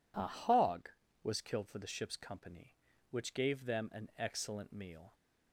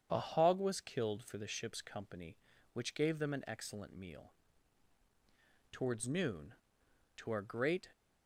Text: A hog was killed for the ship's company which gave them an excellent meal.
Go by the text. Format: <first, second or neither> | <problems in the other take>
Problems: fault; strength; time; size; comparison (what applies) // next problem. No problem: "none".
first | starts louder than the rest; strong; until 1.1 s; 8 dB // goes on to say "Towards noon to our great"; strong; from 5.7 s on; 2.1 s long